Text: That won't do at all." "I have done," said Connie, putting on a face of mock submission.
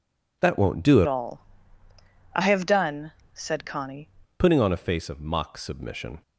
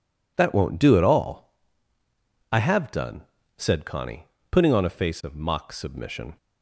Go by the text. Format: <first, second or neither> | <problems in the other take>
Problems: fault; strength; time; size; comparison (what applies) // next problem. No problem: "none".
second | changes voice from "all" to "Connie"; from 1.0 to 4.0 s; 3.0 s long